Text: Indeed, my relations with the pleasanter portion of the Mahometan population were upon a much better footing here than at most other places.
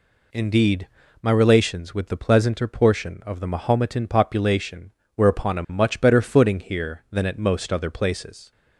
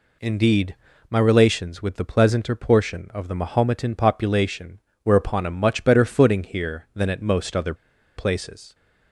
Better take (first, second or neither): first